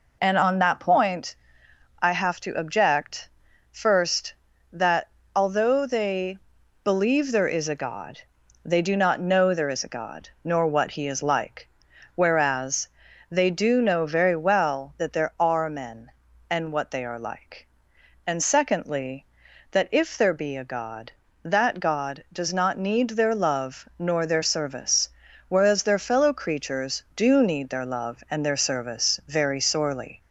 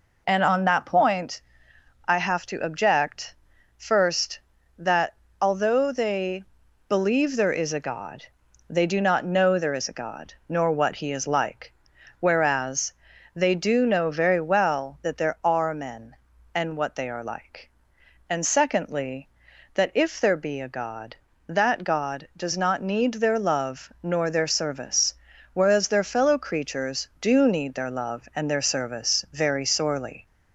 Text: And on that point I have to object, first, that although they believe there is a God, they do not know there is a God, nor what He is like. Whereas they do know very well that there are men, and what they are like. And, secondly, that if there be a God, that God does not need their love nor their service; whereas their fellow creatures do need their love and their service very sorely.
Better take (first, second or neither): neither